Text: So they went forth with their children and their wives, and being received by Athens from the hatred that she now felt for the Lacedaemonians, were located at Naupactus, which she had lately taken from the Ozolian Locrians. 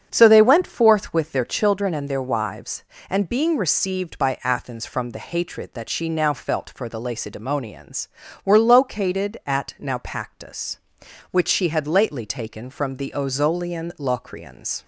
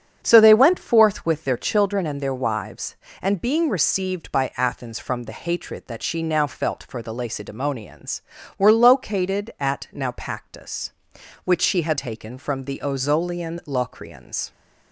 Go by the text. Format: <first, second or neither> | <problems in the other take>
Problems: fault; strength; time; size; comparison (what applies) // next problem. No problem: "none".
first | starts louder than the rest; strong; until 1.2 s; 8 dB; strong in the first // skips "lately"; at 11.9 s